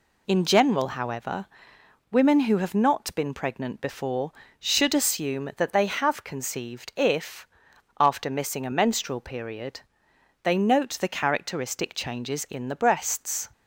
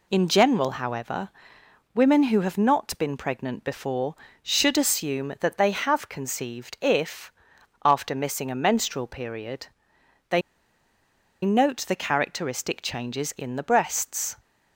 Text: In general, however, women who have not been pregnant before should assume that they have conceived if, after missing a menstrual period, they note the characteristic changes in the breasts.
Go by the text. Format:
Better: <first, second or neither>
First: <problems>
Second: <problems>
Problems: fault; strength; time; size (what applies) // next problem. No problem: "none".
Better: first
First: none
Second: pauses between "they" and "note"; at 10.4 s; 1.0 s long